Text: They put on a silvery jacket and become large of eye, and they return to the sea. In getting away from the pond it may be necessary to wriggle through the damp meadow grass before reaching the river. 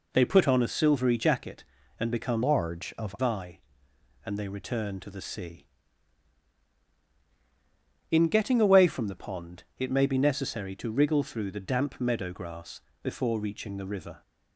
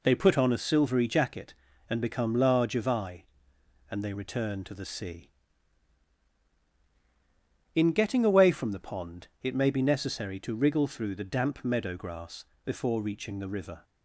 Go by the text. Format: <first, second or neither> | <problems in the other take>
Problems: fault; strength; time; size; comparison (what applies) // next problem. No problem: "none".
second | changes voice from "large" to "of"; from 2.4 to 3.1 s; 0.7 s long // pauses between "grass" and "before"; slight; at 12.8 s; 0.20 s long; slight in the second